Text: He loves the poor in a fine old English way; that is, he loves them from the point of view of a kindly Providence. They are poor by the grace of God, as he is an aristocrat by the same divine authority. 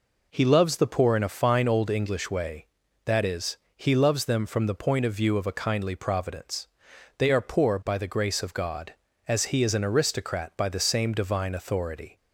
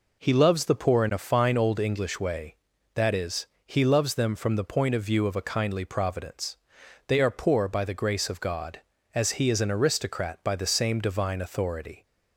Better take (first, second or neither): neither